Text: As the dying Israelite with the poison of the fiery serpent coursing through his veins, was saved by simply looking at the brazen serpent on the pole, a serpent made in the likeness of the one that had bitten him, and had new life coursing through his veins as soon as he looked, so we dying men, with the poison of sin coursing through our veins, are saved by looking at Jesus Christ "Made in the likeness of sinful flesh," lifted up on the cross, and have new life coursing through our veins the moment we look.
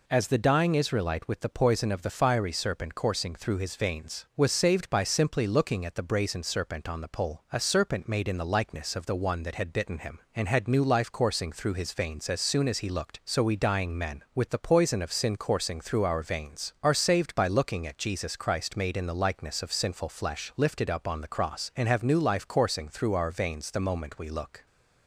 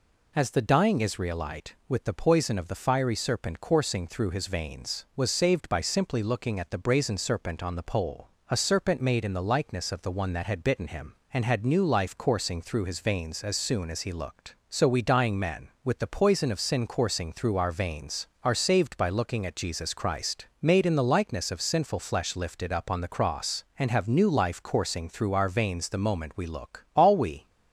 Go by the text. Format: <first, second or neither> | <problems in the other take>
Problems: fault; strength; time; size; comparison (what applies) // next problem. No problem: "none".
first | pauses between "Christ" and "Made"; slight; at 20.4 s; 0.16 s long // goes on to say "All we"; from 26.9 s on; 0.54 s long